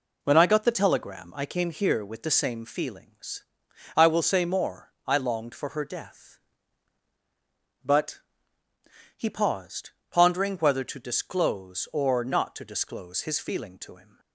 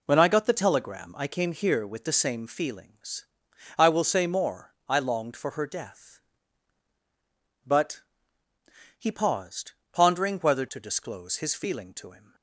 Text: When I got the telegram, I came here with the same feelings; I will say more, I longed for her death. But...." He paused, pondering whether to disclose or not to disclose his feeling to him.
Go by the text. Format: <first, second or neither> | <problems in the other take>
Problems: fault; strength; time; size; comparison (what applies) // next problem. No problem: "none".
first | skips "to disclose or not"; at 10.6 s